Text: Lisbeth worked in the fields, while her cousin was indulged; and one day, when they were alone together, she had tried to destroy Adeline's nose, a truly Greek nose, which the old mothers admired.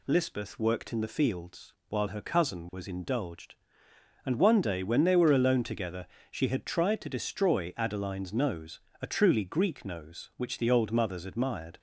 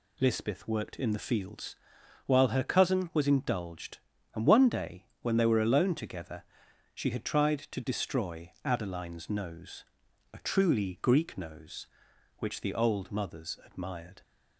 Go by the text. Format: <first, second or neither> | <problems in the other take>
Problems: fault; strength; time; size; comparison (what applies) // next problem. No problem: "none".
neither | none